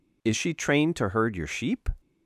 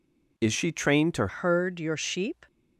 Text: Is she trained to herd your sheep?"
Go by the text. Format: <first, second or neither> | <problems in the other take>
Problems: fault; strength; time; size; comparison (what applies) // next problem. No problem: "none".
first | changes voice at "herd"; from 1.2 s on; 1.2 s long